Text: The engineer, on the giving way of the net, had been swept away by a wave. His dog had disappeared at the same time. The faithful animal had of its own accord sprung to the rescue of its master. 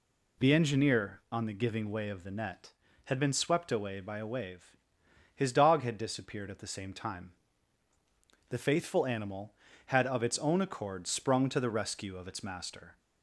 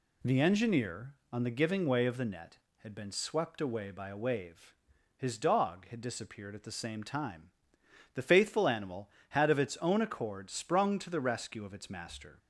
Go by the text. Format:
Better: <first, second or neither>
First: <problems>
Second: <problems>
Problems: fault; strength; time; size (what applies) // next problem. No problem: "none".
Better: neither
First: none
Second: none